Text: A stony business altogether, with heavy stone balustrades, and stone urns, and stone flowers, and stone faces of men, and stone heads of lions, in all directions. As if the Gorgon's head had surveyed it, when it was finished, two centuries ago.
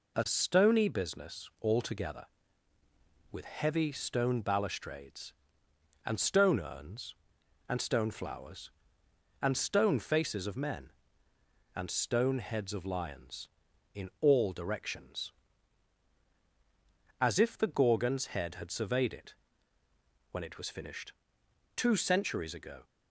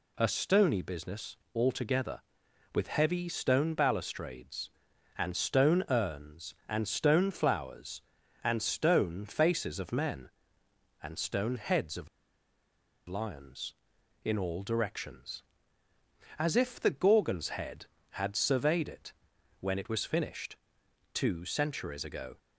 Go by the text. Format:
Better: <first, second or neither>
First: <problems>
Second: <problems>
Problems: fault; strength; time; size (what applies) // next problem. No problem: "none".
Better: first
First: none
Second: pauses between "business" and "altogether"; slight; at 1.3 s; 0.18 s long // pauses between "of" and "lions"; at 12.0 s; 1.0 s long